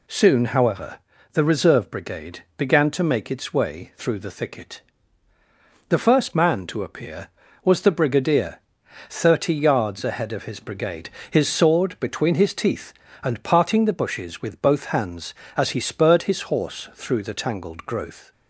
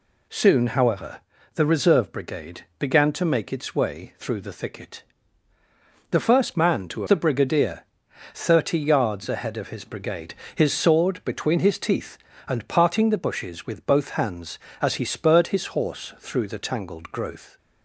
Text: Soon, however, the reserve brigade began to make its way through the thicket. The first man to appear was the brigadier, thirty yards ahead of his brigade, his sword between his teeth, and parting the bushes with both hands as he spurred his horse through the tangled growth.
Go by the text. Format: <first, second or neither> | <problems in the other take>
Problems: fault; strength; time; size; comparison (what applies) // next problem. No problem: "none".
first | skips "appear was"; at 7.0 s